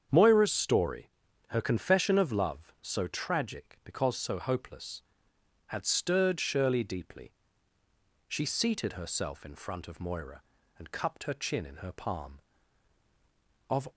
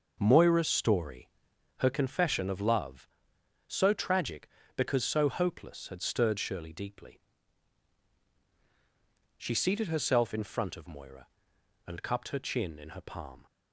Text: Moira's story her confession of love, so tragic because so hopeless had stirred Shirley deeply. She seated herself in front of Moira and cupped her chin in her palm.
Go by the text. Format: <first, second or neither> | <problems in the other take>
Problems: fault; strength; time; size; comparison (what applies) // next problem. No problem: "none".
second | starts louder than the rest; strong; until 1.5 s; 8 dB // pauses between "story" and "her"; at 1.0 s; 0.44 s long; noticeable in the second // goes on to say "Of"; slight; from 13.6 s on; 0.20 s long